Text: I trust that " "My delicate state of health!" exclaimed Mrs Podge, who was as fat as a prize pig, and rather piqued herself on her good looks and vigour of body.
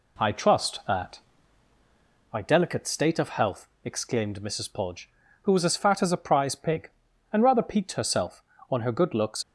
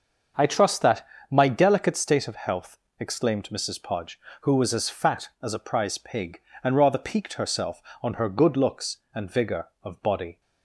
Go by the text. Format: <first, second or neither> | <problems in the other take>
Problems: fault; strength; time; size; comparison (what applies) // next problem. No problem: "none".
second | stops before "and vigour of body"; at 9.4 s